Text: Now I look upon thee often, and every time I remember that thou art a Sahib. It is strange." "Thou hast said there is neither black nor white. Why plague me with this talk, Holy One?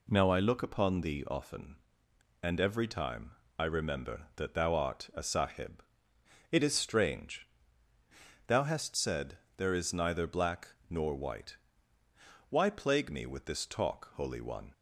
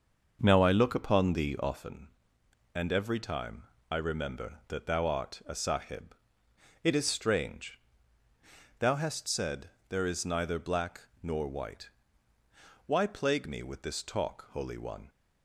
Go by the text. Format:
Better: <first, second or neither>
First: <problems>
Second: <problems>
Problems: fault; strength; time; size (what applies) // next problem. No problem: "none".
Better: first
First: pauses between "time" and "I"; slight; at 3.3 s; 0.26 s long // pauses between "said" and "there"; slight; at 9.3 s; 0.22 s long // pauses between "black" and "nor"; slight; at 10.6 s; 0.20 s long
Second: starts louder than the rest; until 1.9 s; 6.5 dB // pauses between "time" and "I"; slight; at 3.6 s; 0.26 s long // pauses between "said" and "there"; slight; at 9.6 s; 0.22 s long // pauses between "black" and "nor"; slight; at 11.0 s; 0.20 s long